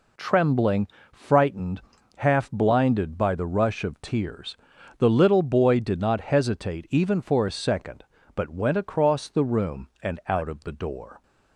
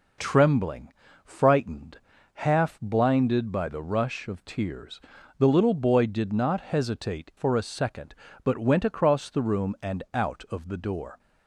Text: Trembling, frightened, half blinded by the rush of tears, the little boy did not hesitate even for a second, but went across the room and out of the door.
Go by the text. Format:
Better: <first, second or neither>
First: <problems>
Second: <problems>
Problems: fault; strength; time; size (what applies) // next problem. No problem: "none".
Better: first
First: none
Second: skips "even"; at 7.3 s